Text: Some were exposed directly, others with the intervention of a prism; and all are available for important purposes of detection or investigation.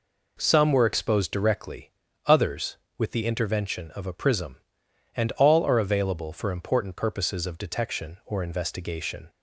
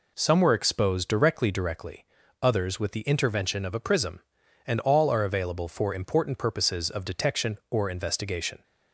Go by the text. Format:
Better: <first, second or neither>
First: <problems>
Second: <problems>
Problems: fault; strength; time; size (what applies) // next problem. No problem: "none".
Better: first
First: none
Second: says "directly" twice; at 1.5 s